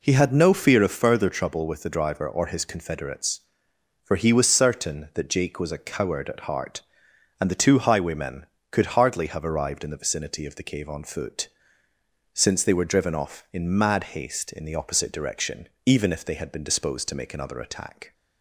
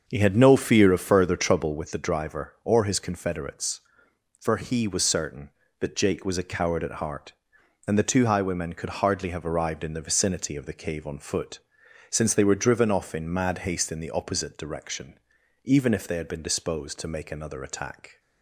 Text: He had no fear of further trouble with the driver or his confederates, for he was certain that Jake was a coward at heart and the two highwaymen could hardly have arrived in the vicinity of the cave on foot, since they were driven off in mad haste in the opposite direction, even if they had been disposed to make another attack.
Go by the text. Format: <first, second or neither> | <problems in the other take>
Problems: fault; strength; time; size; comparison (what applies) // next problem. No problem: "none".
first | starts louder than the rest; until 2.0 s; 6.5 dB